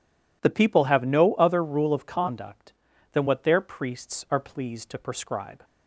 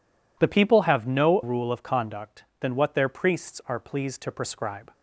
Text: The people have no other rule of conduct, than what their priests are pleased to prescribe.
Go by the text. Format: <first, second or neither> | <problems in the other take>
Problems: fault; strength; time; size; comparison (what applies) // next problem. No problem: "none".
first | skips "other"; at 1.4 s